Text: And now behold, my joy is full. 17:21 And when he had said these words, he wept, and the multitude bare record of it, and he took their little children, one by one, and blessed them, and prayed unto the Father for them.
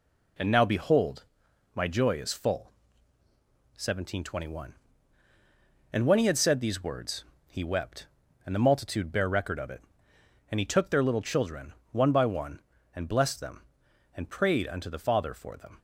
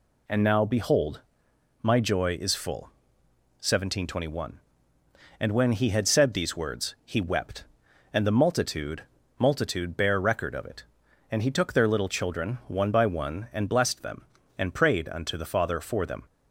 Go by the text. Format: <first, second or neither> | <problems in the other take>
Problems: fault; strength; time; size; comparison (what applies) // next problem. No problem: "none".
first | says "multitude" twice; at 9.3 s